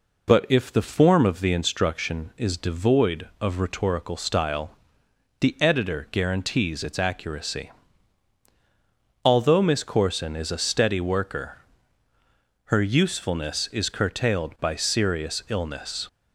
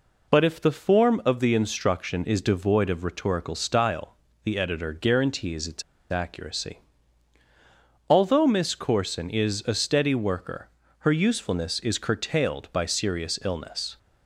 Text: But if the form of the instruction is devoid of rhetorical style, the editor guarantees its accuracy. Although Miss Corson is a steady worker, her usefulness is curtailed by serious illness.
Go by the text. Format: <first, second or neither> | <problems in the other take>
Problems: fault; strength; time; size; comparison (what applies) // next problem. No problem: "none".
first | pauses between "its" and "accuracy"; slight; at 5.8 s; 0.29 s long